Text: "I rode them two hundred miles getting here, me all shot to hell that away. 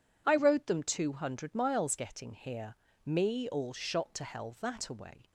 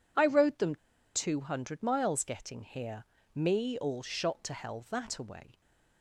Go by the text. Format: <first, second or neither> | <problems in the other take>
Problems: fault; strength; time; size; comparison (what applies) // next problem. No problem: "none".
first | pauses between "them" and "two"; at 0.7 s; 0.38 s long